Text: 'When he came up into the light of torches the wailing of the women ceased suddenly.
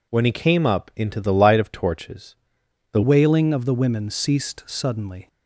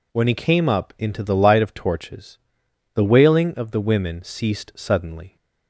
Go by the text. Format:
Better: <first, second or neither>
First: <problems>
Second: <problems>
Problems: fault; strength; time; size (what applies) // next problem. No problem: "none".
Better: second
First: pauses between "torches" and "the"; noticeable; at 2.3 s; 0.56 s long // changes voice at "wailing"; from 3.0 s on; 2.2 s long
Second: pauses between "torches" and "the"; noticeable; at 2.3 s; 0.56 s long